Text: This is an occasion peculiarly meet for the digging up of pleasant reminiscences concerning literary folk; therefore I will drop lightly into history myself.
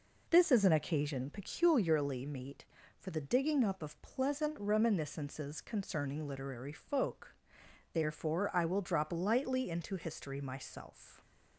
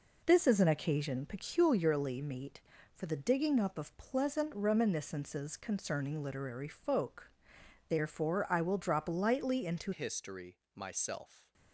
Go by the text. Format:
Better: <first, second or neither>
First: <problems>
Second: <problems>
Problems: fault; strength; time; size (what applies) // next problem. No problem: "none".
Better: first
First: none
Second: changes voice at "history"; from 9.9 s on; 1.6 s long // pauses between "history" and "myself"; slight; at 10.5 s; 0.16 s long